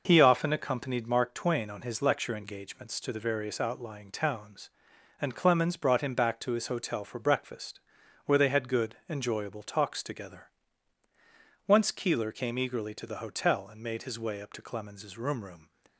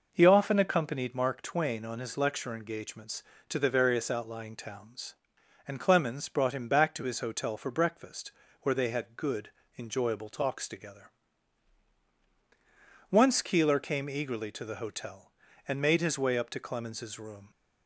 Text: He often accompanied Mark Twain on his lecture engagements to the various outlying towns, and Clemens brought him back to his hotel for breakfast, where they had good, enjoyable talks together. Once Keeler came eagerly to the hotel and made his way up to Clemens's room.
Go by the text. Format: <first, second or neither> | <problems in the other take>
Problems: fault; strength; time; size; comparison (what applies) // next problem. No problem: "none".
second | says "room" twice; at 15.4 s